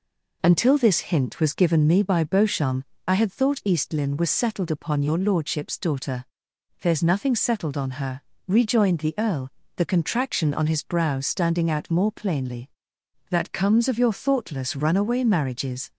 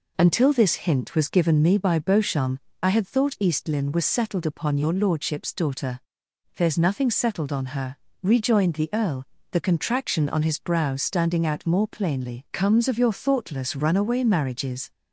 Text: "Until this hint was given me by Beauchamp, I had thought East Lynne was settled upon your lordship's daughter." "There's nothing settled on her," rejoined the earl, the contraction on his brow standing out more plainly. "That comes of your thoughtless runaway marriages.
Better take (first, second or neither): first